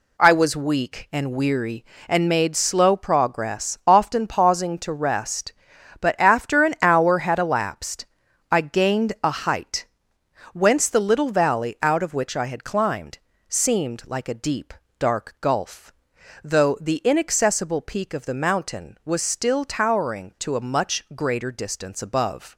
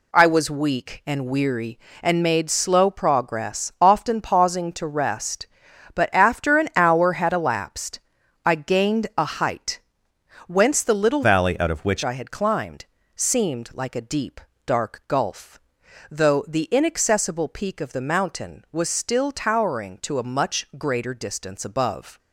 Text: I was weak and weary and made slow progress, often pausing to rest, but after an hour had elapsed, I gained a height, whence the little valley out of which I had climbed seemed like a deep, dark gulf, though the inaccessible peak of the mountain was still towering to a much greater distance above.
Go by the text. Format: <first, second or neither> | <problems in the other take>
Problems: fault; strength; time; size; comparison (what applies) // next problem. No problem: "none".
first | changes voice from "valley" to "which"; from 11.2 to 12.0 s; 0.8 s long // pauses between "climbed" and "seemed"; slight; at 12.8 s; 0.30 s long; slight in the first